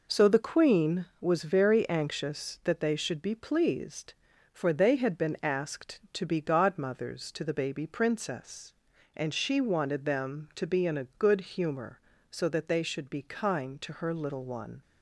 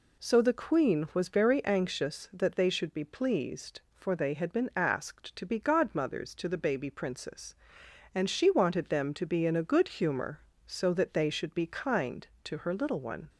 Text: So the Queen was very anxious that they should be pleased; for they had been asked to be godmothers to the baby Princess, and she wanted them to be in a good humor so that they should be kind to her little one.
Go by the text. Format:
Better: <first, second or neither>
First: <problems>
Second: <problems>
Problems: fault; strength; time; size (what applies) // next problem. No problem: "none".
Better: neither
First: none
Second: none